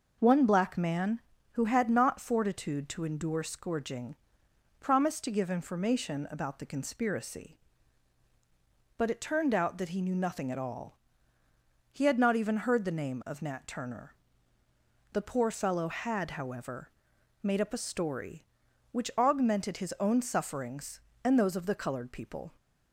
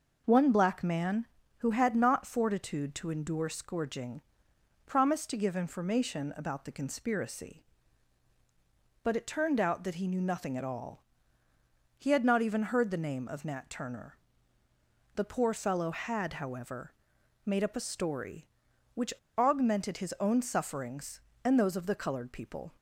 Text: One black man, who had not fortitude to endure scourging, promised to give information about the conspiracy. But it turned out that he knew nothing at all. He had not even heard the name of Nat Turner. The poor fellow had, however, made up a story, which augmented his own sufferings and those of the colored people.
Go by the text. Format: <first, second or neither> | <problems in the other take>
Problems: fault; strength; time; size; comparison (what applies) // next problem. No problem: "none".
first | pauses between "which" and "augmented"; slight; at 19.1 s; 0.25 s long